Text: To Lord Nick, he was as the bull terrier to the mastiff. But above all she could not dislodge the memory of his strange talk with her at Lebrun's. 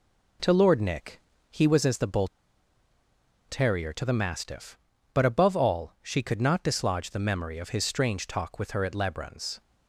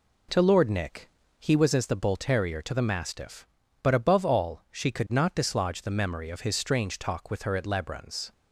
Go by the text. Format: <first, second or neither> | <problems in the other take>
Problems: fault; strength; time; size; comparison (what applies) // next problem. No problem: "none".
second | pauses between "bull" and "terrier"; at 2.2 s; 1.2 s long